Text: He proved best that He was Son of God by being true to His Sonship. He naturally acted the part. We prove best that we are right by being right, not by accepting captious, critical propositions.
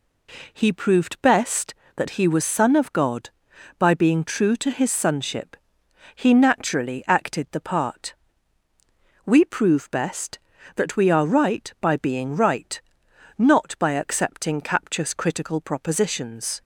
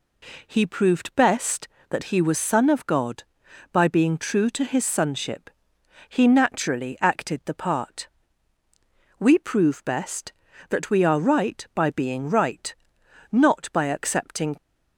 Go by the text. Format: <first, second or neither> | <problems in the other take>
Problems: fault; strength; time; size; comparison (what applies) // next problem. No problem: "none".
first | stops before "captious critical propositions"; at 14.5 s